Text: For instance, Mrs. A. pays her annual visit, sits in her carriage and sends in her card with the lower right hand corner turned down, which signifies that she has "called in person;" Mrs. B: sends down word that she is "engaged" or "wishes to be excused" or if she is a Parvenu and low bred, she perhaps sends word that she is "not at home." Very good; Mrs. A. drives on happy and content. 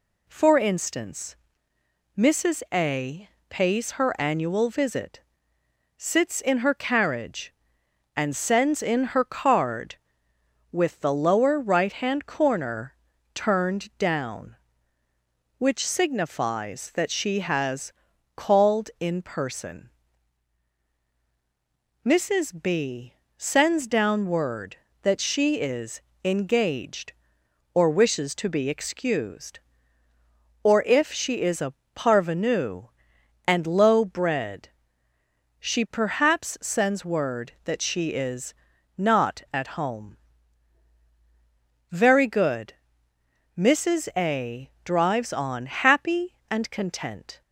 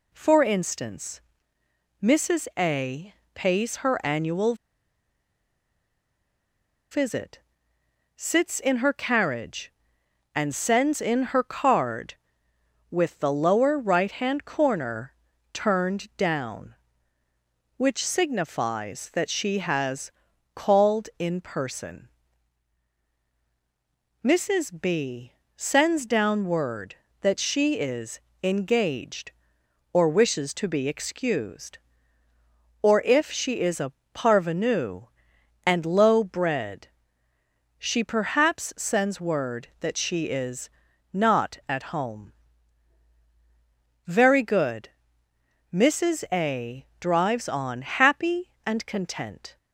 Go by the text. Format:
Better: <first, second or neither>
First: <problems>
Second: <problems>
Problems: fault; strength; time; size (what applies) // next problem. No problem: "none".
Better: first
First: pauses between "A" and "pays"; slight; at 3.2 s; 0.20 s long // pauses between "corner" and "turned"; at 12.9 s; 0.40 s long // pauses between "has" and "called"; at 17.9 s; 0.44 s long // pauses between "is" and "engaged"; slight; at 26.0 s; 0.24 s long // pauses between "a" and "Parvenu"; slight; at 31.7 s; 0.24 s long // pauses between "is" and "not"; at 38.5 s; 0.42 s long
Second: pauses between "A" and "pays"; slight; at 3.1 s; 0.20 s long // pauses between "annual" and "visit"; strong; at 4.5 s; 2.3 s long // pauses between "corner" and "turned"; at 15.1 s; 0.40 s long // pauses between "has" and "called"; at 20.1 s; 0.44 s long // pauses between "is" and "engaged"; slight; at 28.1 s; 0.24 s long // pauses between "a" and "Parvenu"; slight; at 33.9 s; 0.24 s long // pauses between "is" and "not"; at 40.6 s; 0.42 s long